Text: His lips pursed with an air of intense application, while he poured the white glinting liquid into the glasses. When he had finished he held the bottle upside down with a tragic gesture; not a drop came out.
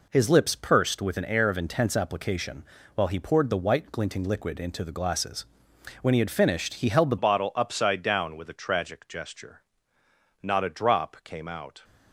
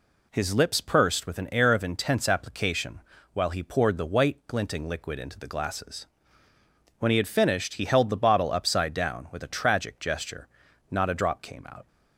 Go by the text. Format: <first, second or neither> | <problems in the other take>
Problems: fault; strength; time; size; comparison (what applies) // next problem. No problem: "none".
second | changes voice at "bottle"; from 7.1 s on; 4.7 s long